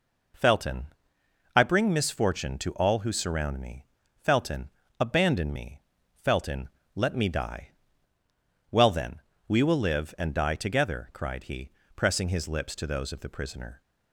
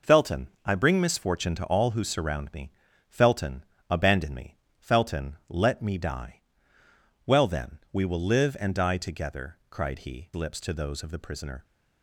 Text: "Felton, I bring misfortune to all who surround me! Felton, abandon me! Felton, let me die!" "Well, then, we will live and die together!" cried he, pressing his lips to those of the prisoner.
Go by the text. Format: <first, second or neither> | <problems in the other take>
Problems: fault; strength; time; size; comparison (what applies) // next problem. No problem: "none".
first | skips "pressing his"; at 10.3 s